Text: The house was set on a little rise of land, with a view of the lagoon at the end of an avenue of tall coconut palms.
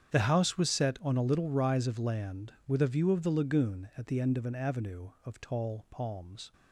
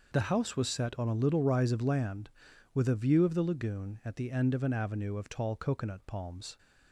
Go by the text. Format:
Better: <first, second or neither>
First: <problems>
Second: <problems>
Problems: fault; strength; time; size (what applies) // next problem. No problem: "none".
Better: second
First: starts louder than the rest; strong; until 1.1 s; 8.5 dB // skips "coconut"; at 5.8 s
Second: none